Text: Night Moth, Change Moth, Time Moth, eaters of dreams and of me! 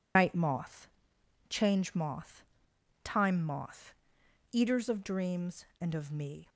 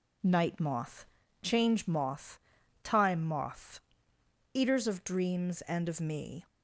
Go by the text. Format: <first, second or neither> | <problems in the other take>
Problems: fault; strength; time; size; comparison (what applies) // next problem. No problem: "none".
second | loses the start of "Night"; at 0.1 s; 105 ms